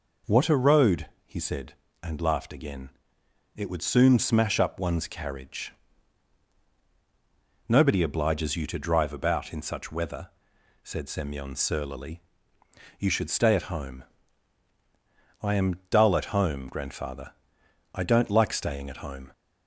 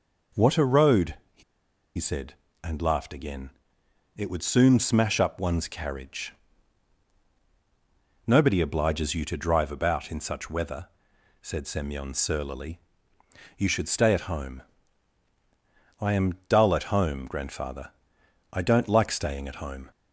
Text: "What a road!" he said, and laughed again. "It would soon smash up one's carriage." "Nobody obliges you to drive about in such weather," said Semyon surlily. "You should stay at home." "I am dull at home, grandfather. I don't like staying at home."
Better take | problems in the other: first | pauses between "he" and "said"; noticeable; at 1.4 s; 0.55 s long

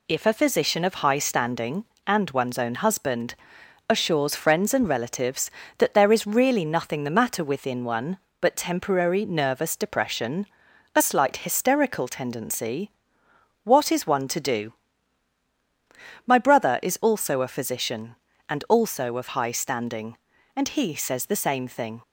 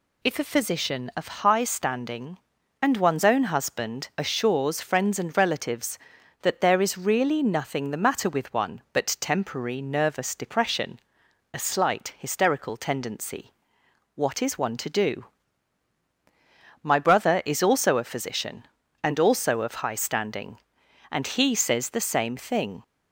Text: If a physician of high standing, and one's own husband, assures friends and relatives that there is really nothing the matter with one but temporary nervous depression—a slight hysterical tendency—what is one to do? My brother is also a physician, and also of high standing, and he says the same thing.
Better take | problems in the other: second | says "within" for "with"; at 7.4 s

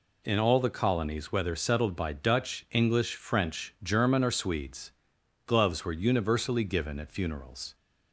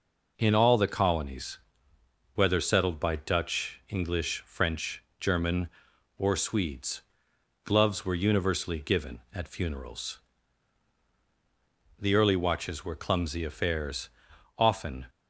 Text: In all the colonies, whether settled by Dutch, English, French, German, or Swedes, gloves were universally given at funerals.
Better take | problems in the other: first | goes on to say "The early watches were clumsy affairs often"; strong; from 11.9 s on; 3.0 s long

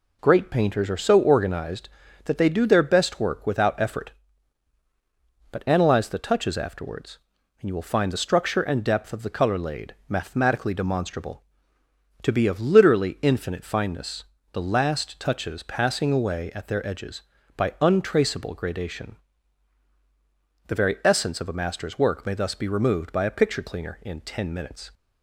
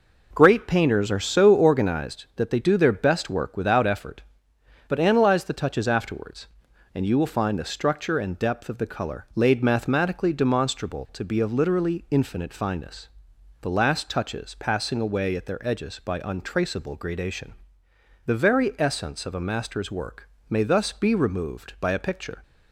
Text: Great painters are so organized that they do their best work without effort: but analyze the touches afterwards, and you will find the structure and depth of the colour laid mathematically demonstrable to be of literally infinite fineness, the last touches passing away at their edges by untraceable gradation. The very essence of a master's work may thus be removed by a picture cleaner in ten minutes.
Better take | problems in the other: first | pauses between "work" and "may"; slight; at 20.2 s; 0.22 s long // stops before "cleaner in ten minutes"; at 22.4 s

